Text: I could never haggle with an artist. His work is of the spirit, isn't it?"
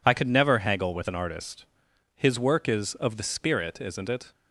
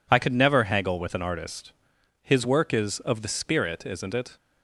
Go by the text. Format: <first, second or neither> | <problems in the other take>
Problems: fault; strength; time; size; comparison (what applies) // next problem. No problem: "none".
neither | none